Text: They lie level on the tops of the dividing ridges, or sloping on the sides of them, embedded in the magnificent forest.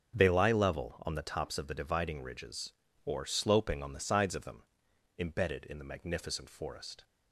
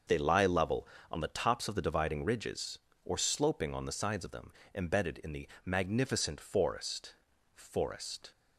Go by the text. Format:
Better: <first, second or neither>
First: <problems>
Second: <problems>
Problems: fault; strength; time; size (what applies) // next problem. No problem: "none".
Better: first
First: starts louder than the rest; noticeable; until 1.1 s; 6 dB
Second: starts louder than the rest; until 1.3 s; 6.5 dB // pauses between "the" and "magnificent"; slight; at 5.4 s; 0.16 s long // says "forest" twice; at 7.5 s